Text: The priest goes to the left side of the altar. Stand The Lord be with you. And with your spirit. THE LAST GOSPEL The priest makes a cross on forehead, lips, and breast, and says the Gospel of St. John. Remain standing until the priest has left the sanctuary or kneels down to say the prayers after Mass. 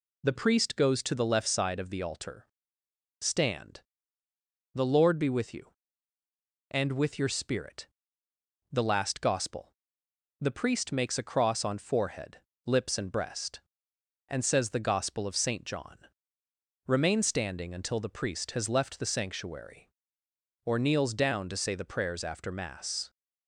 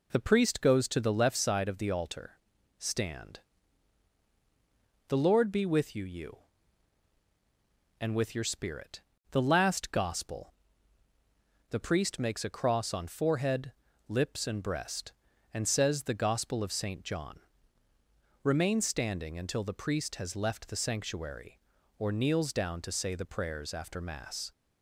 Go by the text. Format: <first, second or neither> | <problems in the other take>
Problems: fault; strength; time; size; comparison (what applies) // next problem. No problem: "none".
first | pauses between "Stand" and "The"; strong; at 3.3 s; 1.6 s long; noticeable in the first // says "you" twice; at 6.0 s // pauses between "GOSPEL" and "The"; at 10.5 s; 1.1 s long; noticeable in the first